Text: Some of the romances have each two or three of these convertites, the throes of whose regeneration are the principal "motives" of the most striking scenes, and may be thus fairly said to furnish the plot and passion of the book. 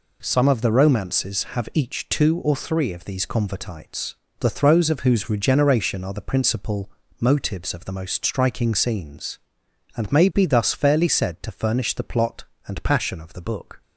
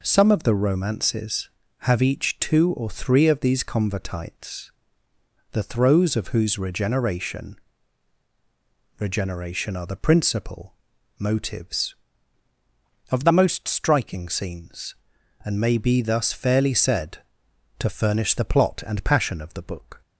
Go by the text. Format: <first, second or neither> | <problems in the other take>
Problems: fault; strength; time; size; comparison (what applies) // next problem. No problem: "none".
first | says "regeneration" twice; at 8.9 s // pauses between "principal" and "motives"; noticeable; at 10.7 s; 0.46 s long; slight in the first